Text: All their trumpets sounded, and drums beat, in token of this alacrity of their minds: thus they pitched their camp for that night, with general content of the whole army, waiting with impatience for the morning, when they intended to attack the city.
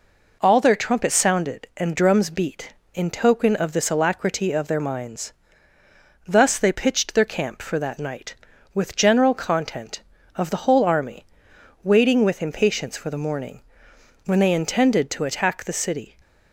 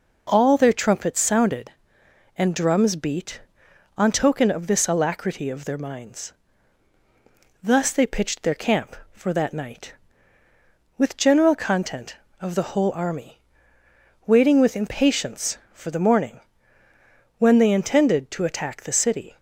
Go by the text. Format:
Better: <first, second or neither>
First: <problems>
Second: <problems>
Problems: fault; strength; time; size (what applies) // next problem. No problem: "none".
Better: first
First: none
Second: says "on" for "in"; at 3.9 s